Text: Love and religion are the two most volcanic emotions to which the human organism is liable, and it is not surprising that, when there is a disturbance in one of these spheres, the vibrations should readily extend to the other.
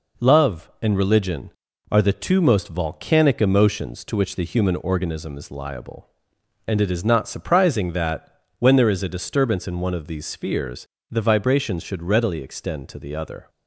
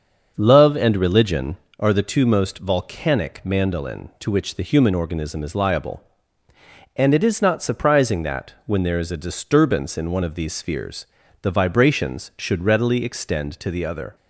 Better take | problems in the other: first | starts louder than the rest; until 1.3 s; 6.5 dB // says "mandolin" for "emotions"; at 3.4 s

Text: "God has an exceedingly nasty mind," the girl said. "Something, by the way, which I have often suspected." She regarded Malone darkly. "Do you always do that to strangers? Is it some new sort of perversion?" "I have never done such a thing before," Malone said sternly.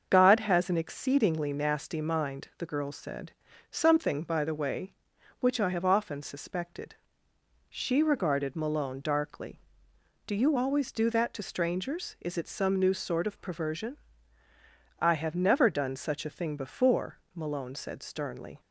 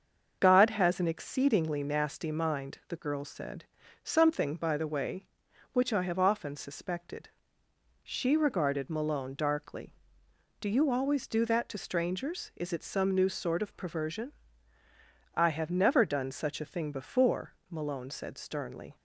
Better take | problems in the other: neither | starts louder than the rest; the same in both

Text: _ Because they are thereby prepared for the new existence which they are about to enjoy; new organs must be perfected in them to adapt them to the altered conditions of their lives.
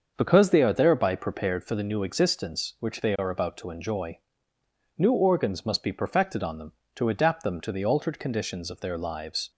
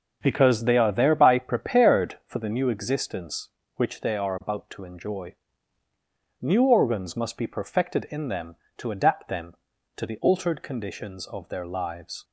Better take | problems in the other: second | starts louder than the rest; until 1.1 s; 6.5 dB // says "on" for "in"; at 6.4 s

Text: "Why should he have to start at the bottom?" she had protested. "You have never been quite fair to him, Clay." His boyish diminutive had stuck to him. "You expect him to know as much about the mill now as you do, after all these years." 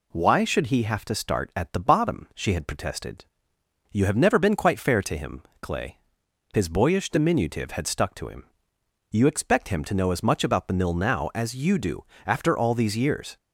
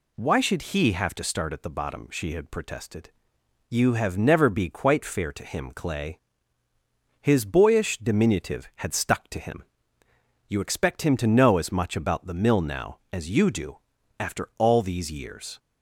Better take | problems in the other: first | says "be" for "been"; at 4.4 s

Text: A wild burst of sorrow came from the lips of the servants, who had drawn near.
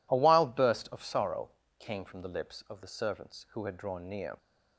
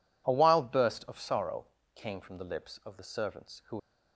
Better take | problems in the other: first | pauses between "sorrow" and "came"; slight; at 1.6 s; 0.26 s long; slight in the first // stops before "had drawn near"; at 3.7 s

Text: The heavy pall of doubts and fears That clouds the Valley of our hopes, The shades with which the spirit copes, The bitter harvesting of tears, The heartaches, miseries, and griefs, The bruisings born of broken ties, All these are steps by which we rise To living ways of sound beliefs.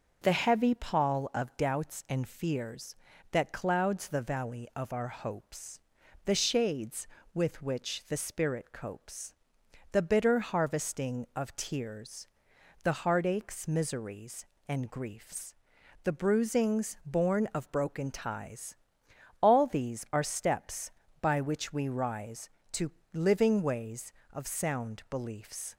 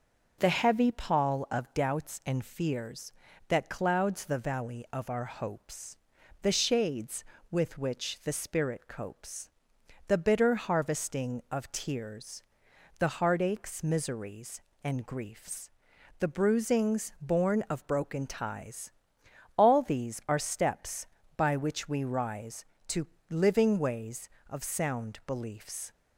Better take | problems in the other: neither | pauses between "To" and "living"; slight; the same in both

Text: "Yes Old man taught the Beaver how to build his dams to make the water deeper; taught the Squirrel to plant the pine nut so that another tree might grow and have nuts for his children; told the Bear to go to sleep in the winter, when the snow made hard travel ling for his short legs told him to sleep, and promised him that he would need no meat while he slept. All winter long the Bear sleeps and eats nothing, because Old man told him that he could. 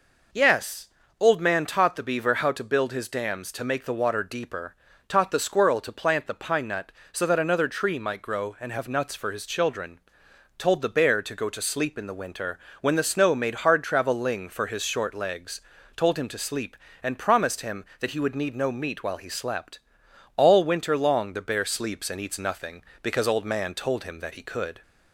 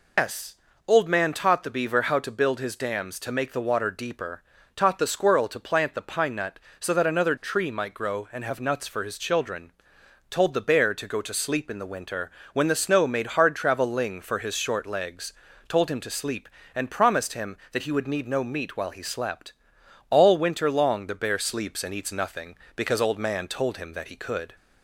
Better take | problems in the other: first | loses the start of "Yes"; at 0.1 s; 170 ms // pauses between "Yes" and "Old"; slight; at 0.5 s; 0.30 s long; slight in the first // pauses between "legs" and "told"; slight; at 15.3 s; 0.34 s long; slight in the first

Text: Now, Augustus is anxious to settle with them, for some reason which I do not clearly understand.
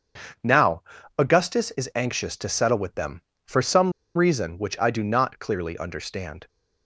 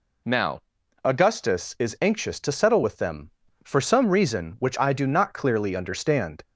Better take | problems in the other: second | starts louder than the rest; strong; until 1.7 s; 7 dB // pauses between "some" and "reason"; slight; at 3.9 s; 0.23 s long

